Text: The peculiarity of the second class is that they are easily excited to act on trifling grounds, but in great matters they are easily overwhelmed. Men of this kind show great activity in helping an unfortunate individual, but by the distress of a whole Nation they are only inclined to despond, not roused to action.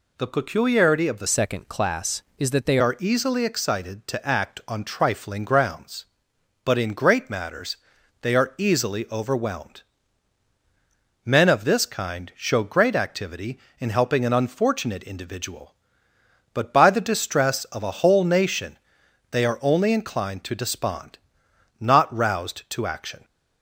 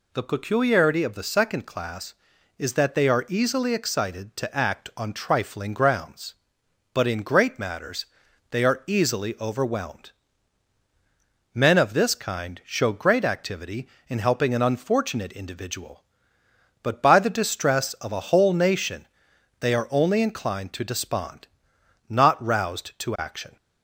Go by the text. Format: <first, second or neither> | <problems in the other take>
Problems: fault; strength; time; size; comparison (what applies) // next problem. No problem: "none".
second | changes voice from "second" to "they"; from 1.2 to 2.7 s; 1.5 s long // pauses between "matters" and "they"; at 7.7 s; 0.44 s long; also in the second // pauses between "Nation" and "they"; noticeable; at 18.7 s; 0.54 s long; noticeable in the second